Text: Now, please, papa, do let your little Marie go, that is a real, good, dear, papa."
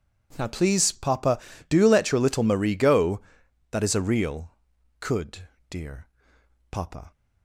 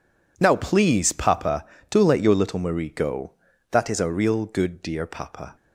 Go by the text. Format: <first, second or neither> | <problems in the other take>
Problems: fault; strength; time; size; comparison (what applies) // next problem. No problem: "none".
second | says "could" for "good"; at 4.9 s